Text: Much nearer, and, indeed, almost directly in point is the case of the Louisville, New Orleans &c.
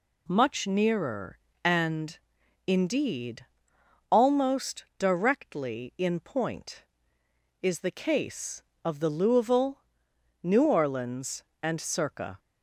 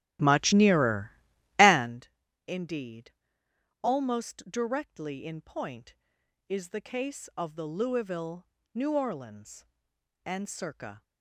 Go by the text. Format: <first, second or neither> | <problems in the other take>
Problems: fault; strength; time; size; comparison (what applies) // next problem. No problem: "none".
first | starts louder than the rest; strong; until 2.1 s; 15 dB